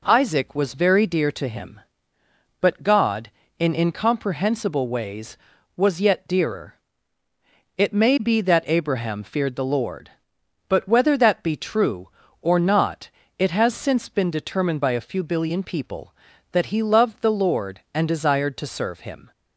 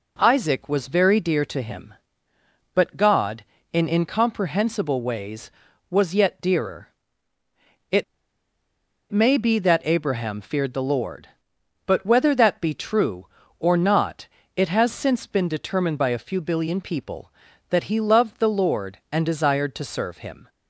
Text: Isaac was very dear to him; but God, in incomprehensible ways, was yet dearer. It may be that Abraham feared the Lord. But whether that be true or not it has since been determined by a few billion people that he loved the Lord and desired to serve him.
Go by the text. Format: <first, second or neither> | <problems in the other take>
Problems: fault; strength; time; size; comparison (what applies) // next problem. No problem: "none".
first | pauses between "It" and "may"; at 8.0 s; 1.0 s long // pauses between "not" and "it"; slight; at 14.2 s; 0.30 s long; slight in the first